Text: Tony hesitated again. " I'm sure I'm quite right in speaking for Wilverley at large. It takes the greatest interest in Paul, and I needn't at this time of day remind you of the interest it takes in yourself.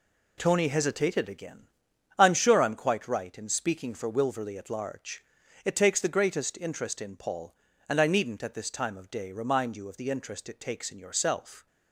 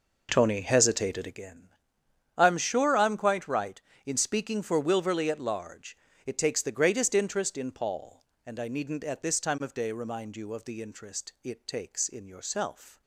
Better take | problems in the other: first | starts louder than the rest; noticeable; until 1.4 s; 5 dB

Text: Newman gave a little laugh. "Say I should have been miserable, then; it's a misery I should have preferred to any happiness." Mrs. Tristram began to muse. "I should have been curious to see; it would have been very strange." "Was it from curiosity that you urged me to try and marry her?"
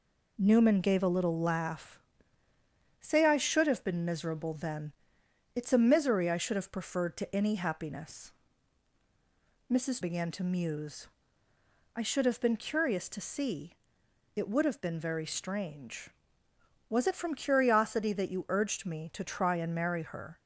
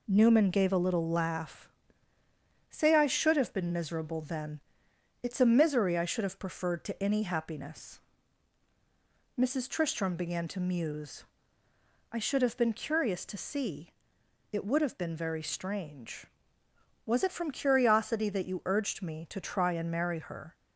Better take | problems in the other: second | skips "Tristram"; at 10.0 s

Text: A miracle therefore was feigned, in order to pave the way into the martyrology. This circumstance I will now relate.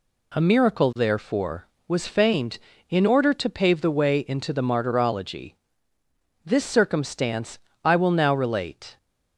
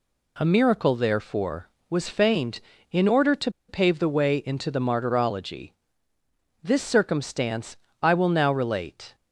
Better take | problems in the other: first | pauses between "to" and "pave"; slight; at 3.5 s; 0.17 s long // pauses between "circumstance" and "I"; slight; at 7.7 s; 0.28 s long; slight in the first

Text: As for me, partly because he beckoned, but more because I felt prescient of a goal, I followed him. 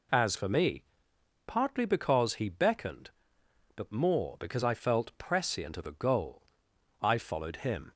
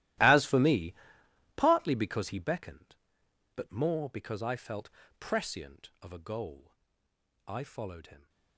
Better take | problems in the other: first | gets quieter; strong; throughout; 18.5 dB // pauses between "felt" and "prescient"; slight; at 4.8 s; 0.30 s long

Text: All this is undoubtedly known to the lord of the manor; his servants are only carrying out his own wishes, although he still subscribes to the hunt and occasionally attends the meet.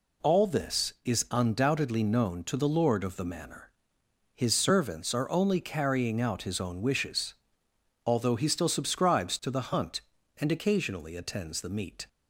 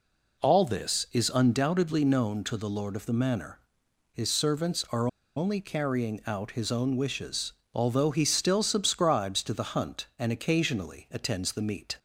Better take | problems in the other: first | pauses between "are" and "only"; slight; at 5.0 s; 0.28 s long

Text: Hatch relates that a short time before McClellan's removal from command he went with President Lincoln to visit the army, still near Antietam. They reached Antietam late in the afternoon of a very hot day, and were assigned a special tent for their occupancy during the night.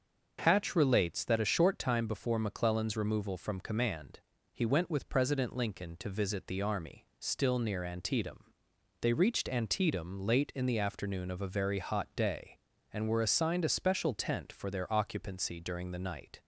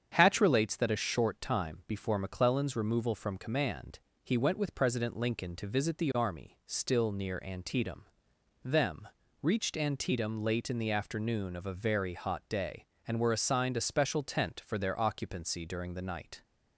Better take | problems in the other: first | starts louder than the rest; strong; until 1.1 s; 8 dB; also in the first // pauses between "command" and "he"; slight; at 3.9 s; 0.24 s long; slight in the first // says "Them" for "They"; at 8.6 s

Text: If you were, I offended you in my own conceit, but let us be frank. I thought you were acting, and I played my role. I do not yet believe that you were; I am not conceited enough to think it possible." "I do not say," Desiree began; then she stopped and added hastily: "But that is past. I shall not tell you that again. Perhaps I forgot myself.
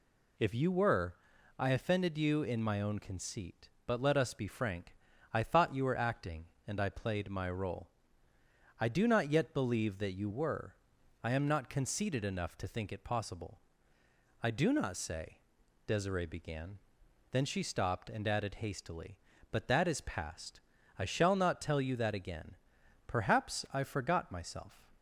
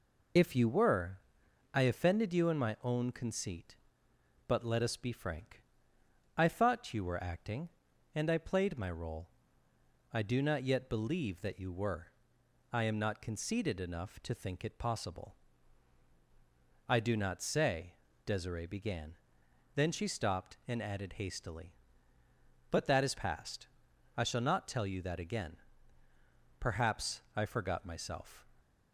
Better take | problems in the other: first | loses the start of "If"; at 0.3 s; 45 ms

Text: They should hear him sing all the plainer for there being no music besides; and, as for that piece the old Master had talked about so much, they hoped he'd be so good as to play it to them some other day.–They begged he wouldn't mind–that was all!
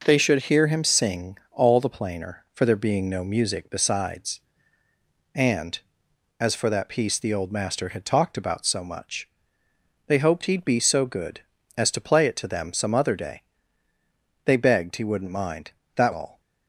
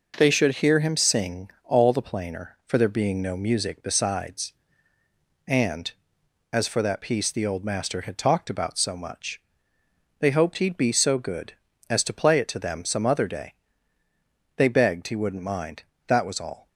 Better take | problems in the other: second | pauses between "sing" and "all"; slight; at 1.3 s; 0.16 s long; slight in the second // skips "was"; at 16.1 s

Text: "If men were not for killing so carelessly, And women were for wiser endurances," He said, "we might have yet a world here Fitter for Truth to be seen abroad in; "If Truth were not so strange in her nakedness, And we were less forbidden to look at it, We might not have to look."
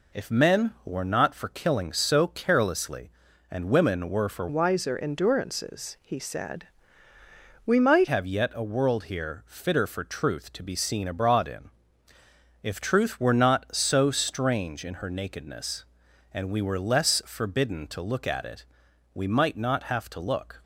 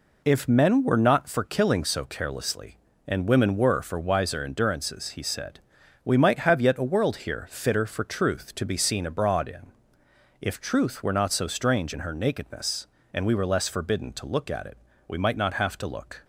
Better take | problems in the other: second | changes voice from "wiser" to "might"; from 4.4 to 8.0 s; 3.6 s long

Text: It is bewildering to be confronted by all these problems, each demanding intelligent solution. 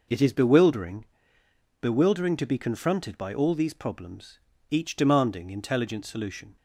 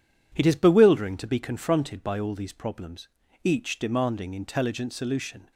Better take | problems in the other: second | says "bewildering" twice; at 1.8 s

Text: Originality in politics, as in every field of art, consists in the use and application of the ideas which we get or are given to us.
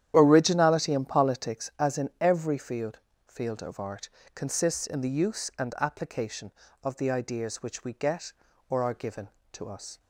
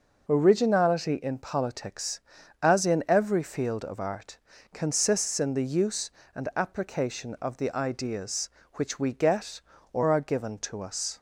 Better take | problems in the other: second | starts louder than the rest; strong; until 1.1 s; 10.5 dB // says "field" twice; at 3.2 s

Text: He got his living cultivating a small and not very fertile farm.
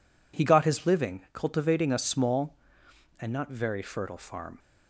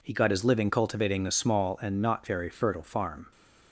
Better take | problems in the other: neither | none

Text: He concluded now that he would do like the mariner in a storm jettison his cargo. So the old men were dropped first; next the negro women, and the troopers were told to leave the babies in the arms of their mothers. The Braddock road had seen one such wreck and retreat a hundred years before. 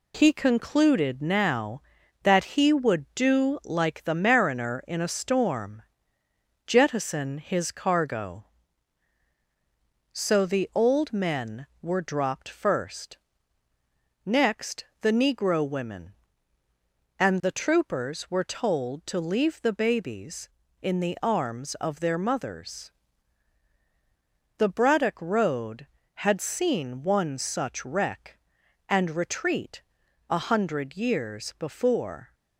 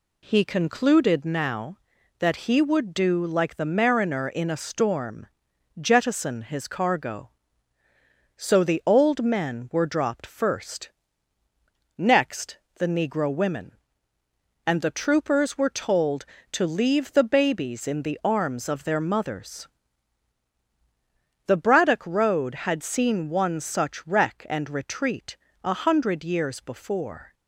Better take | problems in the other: second | gets quieter; noticeable; throughout; 5.5 dB // pauses between "storm" and "jettison"; noticeable; at 5.8 s; 0.84 s long; noticeable in the second // pauses between "next" and "the"; slight; at 14.8 s; 0.16 s long; slight in the second // pauses between "retreat" and "a"; noticeable; at 29.8 s; 0.48 s long; slight in the second

